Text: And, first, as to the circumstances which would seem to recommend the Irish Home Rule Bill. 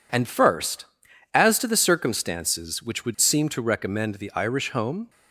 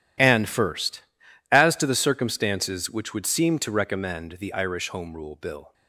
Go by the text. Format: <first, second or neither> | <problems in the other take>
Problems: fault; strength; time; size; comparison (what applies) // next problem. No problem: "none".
second | stops before "Rule Bill"; at 5.0 s